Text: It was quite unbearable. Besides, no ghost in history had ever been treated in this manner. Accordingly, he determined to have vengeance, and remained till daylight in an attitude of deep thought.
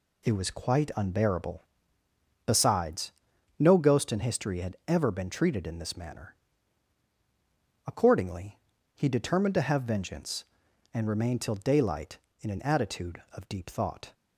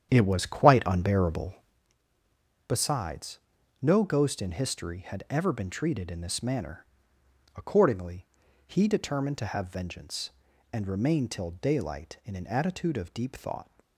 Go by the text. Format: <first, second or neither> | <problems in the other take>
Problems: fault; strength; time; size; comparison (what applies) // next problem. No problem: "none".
first | starts louder than the rest; strong; until 1.8 s; 9 dB